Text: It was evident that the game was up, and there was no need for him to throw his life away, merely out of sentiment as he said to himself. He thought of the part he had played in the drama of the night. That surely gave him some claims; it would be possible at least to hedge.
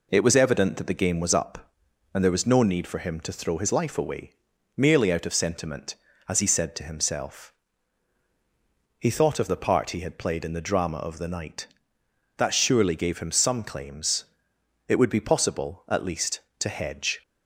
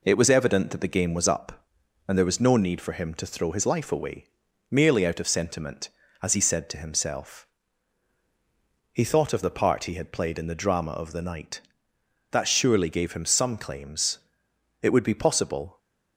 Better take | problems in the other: first | stops before "at least to hedge"; at 15.7 s

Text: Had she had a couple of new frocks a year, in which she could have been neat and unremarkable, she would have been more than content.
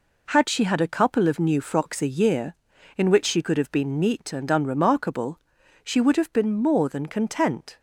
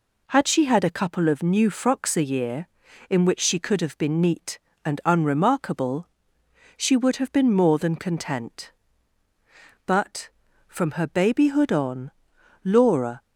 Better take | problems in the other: first | goes on to say "But from her babyhood on Laura"; strong; from 9.8 s on; 3.2 s long

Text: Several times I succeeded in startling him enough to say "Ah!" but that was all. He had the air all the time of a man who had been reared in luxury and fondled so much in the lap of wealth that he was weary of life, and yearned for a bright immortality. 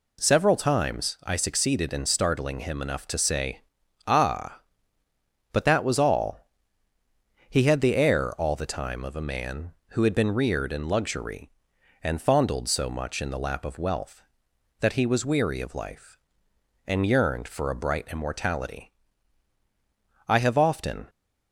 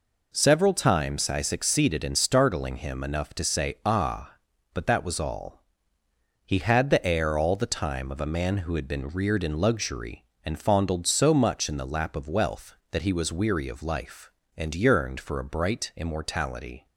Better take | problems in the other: second | pauses between "say" and "Ah"; at 3.6 s; 0.44 s long // goes on to say "I have often"; noticeable; from 20.2 s on; 0.82 s long

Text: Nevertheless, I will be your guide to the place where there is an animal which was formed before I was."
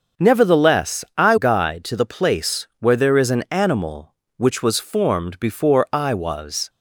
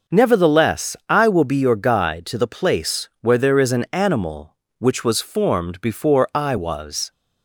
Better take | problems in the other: second | starts louder than the rest; until 1.3 s; 6.5 dB; noticeable in the second // skips "will be your"; at 1.3 s

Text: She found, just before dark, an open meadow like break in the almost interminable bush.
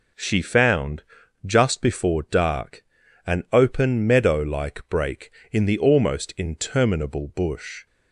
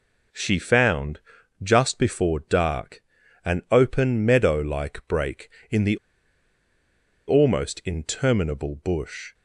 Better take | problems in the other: first | pauses between "the" and "almost"; strong; at 5.9 s; 1.3 s long

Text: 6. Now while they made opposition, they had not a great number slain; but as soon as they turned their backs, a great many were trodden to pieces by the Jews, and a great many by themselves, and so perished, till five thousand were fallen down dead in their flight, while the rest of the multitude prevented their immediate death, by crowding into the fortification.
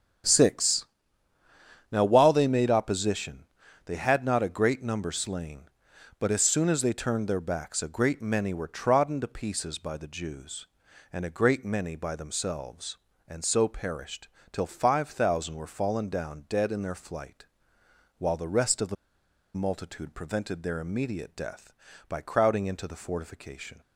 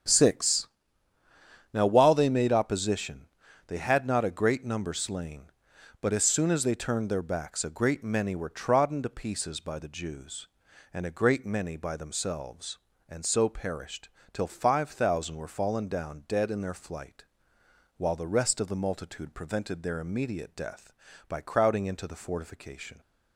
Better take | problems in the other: second | starts louder than the rest; strong; until 2.2 s; 8.5 dB; strong in the second // pauses between "the" and "multitude"; noticeable; at 18.9 s; 0.61 s long

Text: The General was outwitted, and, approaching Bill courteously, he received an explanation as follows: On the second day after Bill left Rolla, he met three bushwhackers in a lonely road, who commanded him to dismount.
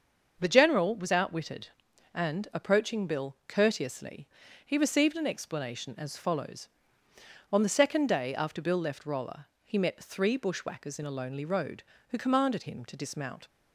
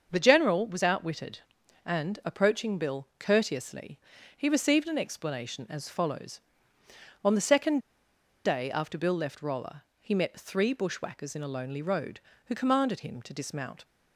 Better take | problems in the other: first | starts louder than the rest; until 1.1 s; 6.5 dB; also in the first // pauses between "second" and "day"; noticeable; at 7.8 s; 0.64 s long

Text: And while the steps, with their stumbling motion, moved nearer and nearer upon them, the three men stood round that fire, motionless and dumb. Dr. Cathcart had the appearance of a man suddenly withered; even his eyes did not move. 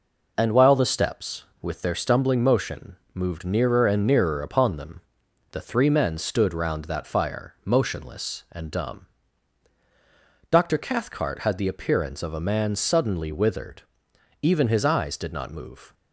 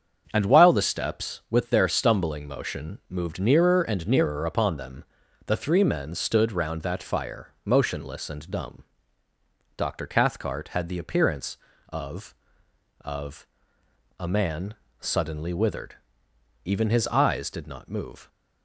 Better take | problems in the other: first | starts louder than the rest; strong; until 1.3 s; 7 dB // says "of" twice; at 13.0 s // pauses between "man" and "suddenly"; slight; at 14.7 s; 0.26 s long

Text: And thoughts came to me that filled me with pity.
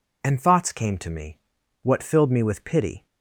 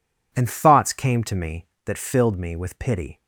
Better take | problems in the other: second | says "what" for "that"; at 1.8 s

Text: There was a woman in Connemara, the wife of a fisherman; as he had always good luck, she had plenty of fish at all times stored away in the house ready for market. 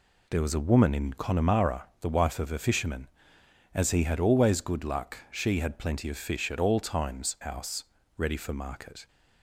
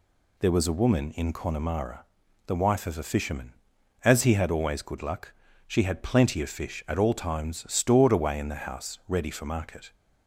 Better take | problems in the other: second | skips "stored away in the"; at 7.3 s // pauses between "house" and "ready"; slight; at 7.8 s; 0.34 s long

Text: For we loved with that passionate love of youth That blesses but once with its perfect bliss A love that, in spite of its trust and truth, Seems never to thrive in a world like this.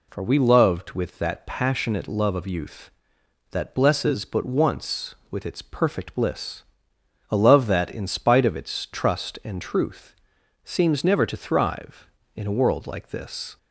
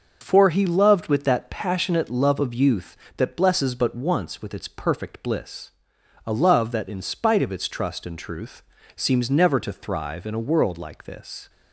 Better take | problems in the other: first | says "he" for "we"; at 0.4 s // pauses between "bliss" and "A"; noticeable; at 5.7 s; 0.56 s long; noticeable in the first

